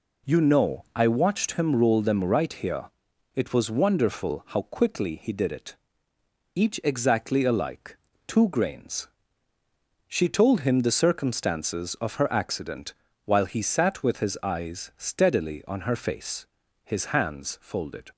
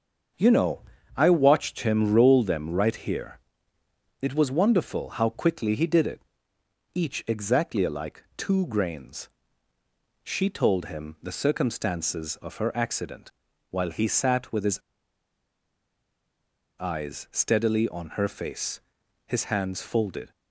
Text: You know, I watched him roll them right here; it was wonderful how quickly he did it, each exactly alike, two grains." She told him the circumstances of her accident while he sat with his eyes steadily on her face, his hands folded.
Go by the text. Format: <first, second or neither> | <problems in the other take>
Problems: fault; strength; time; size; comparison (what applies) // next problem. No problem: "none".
first | starts louder than the rest; until 1.7 s; 7 dB // pauses between "accident" and "while"; at 13.2 s; 0.40 s long; slight in the first // pauses between "his" and "eyes"; strong; at 14.7 s; 1.9 s long